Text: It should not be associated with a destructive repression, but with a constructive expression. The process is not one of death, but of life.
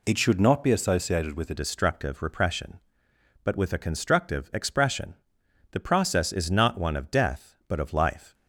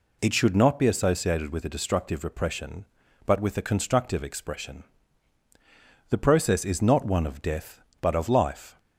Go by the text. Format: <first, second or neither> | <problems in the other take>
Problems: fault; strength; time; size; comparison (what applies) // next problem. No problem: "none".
second | changes voice at "destructive"; from 1.5 s on; 6.8 s long